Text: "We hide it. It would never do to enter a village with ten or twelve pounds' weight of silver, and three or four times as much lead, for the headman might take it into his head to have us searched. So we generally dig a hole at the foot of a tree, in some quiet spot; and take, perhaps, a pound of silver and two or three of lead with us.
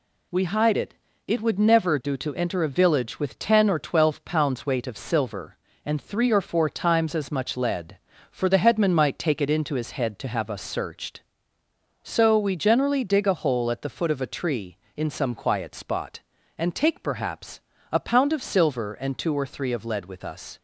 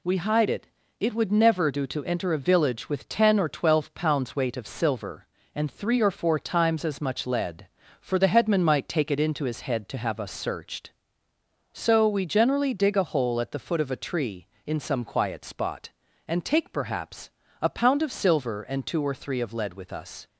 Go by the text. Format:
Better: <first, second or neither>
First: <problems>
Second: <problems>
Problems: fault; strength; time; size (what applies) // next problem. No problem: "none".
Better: neither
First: none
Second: none